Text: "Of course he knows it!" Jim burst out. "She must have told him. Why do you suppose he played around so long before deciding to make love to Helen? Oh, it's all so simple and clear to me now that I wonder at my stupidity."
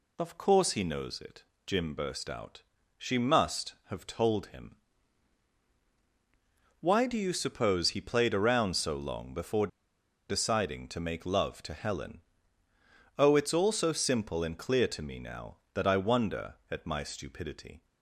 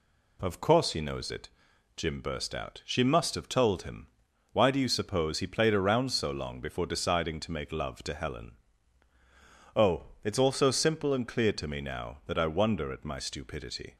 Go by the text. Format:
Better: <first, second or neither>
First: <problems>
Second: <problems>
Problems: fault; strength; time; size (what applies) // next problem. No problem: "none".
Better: second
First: pauses between "before" and "deciding"; noticeable; at 9.6 s; 0.62 s long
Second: none